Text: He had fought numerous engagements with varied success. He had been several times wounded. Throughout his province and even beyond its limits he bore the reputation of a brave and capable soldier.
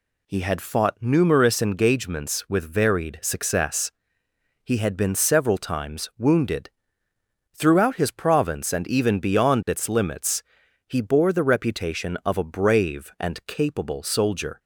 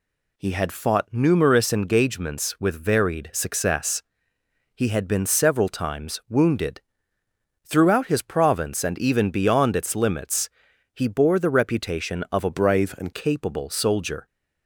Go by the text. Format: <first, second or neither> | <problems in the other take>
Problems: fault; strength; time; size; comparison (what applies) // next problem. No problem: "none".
first | pauses between "limits" and "he"; at 10.4 s; 0.44 s long; also in the first // changes voice from "brave" to "and"; from 12.5 to 13.1 s; 0.6 s long